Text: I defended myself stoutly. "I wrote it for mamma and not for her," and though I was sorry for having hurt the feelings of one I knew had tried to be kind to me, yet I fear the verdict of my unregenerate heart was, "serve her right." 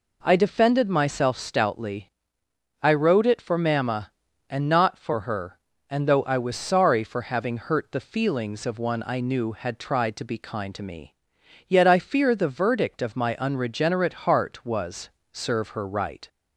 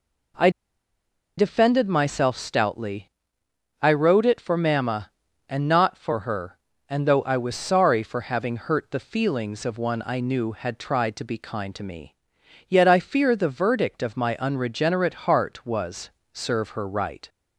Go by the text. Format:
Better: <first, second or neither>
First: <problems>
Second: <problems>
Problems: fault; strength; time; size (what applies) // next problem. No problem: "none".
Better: first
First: none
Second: pauses between "I" and "defended"; noticeable; at 0.4 s; 0.88 s long